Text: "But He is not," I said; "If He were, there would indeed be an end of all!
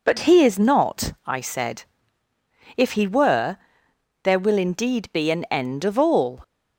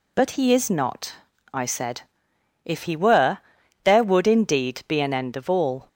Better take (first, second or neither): second